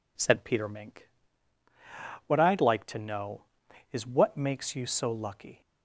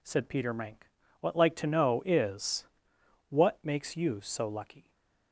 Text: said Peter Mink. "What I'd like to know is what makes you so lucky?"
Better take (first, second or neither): first